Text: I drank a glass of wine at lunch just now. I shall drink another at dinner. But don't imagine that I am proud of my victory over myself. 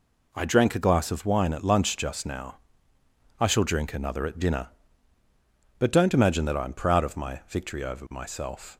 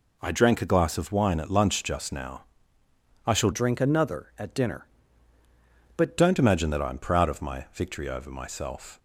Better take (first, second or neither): first